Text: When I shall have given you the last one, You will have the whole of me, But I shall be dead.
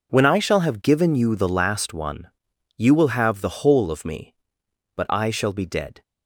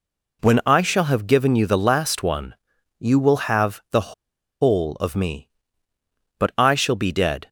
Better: first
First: none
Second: pauses between "the" and "whole"; noticeable; at 4.1 s; 0.47 s long

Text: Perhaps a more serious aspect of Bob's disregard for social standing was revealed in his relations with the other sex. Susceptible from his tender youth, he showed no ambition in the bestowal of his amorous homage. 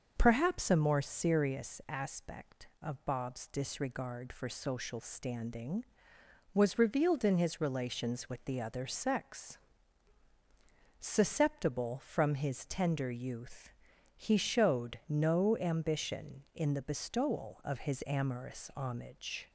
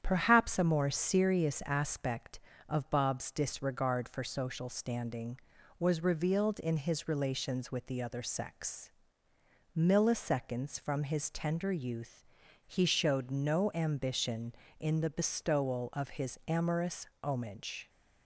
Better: first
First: starts louder than the rest; until 1.1 s; 6.5 dB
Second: starts louder than the rest; strong; until 1.0 s; 9 dB // says "Milliseconds" for "Susceptible"; at 9.7 s // pauses between "amorous" and "homage"; slight; at 17.0 s; 0.16 s long

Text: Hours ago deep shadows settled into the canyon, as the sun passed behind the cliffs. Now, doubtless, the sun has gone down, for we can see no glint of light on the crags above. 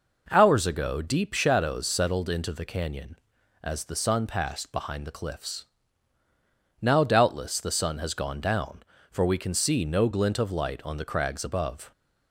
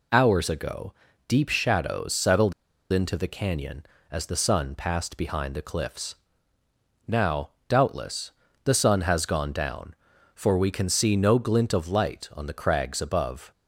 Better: first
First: none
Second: pauses between "ago" and "deep"; slight; at 0.9 s; 0.34 s long // pauses between "settled" and "into"; at 2.5 s; 0.39 s long

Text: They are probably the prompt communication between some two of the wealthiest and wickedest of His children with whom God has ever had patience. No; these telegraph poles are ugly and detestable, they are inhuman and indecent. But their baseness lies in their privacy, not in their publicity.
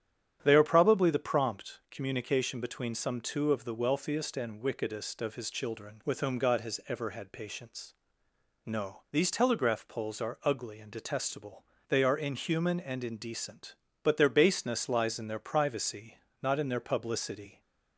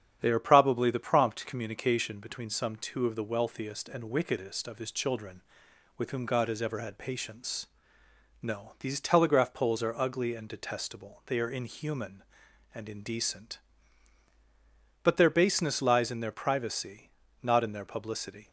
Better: neither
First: starts louder than the rest; strong; until 1.4 s; 9.5 dB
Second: starts louder than the rest; strong; until 1.2 s; 9 dB

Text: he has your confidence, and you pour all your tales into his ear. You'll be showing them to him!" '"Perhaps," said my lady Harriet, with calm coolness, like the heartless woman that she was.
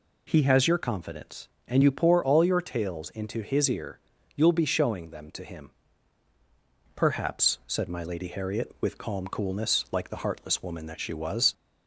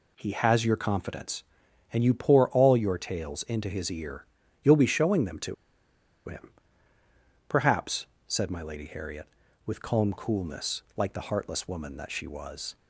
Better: first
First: none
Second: pauses between "to" and "him"; noticeable; at 5.5 s; 0.74 s long

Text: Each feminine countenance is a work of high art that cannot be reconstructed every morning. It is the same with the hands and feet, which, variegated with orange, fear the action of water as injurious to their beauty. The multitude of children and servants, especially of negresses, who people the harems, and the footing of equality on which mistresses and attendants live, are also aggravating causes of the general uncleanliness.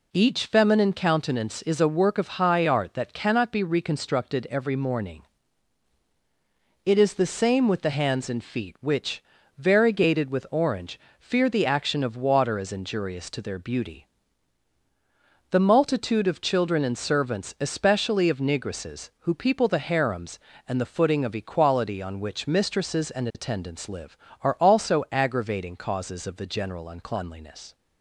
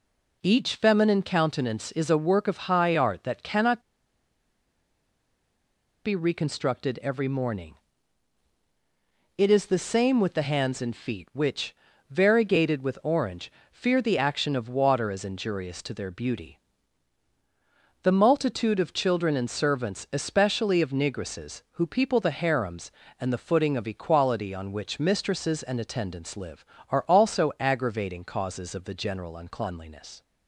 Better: first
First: none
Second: pauses between "cannot" and "be"; strong; at 3.8 s; 2.2 s long

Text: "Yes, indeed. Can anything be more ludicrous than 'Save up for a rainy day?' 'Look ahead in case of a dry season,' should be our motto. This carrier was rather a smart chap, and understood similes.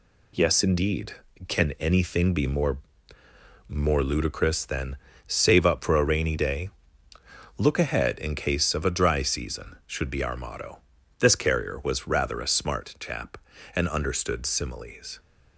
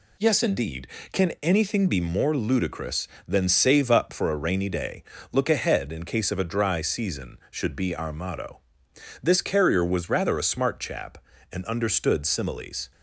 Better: second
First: says "more" twice; at 3.6 s // pauses between "than" and "Save"; slight; at 4.9 s; 0.32 s long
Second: none

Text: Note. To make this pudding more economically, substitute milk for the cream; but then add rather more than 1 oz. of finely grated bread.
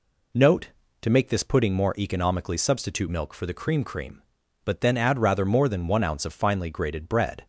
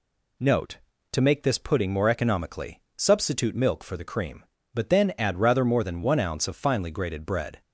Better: second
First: says "cream" twice; at 3.8 s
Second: none

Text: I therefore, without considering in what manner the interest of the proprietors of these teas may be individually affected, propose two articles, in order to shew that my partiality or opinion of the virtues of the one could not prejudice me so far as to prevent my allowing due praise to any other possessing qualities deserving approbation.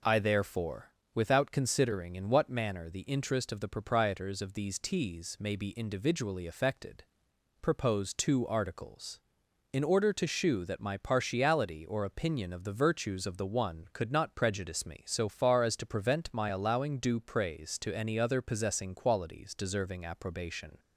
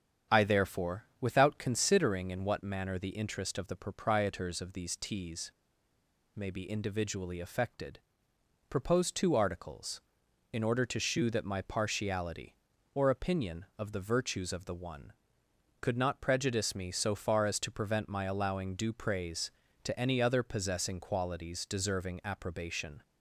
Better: first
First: none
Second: starts louder than the rest; strong; until 1.4 s; 8.5 dB // pauses between "teas" and "may"; noticeable; at 5.5 s; 0.85 s long

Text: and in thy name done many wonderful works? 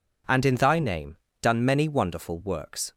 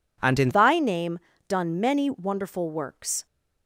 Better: first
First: pauses between "name" and "done"; slight; at 1.1 s; 0.24 s long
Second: changes voice at "thy"; from 0.5 s on; 2.7 s long // pauses between "name" and "done"; slight; at 1.1 s; 0.30 s long

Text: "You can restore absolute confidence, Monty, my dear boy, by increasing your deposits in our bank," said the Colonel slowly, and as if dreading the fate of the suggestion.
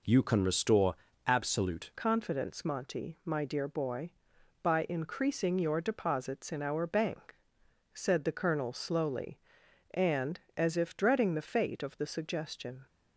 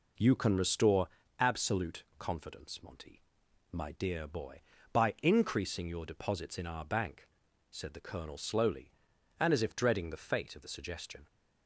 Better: second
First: pauses between "restore" and "absolute"; slight; at 0.9 s; 0.30 s long // changes voice at "confidence"; from 1.9 s on; 10.9 s long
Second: pauses between "restore" and "absolute"; slight; at 1.0 s; 0.30 s long

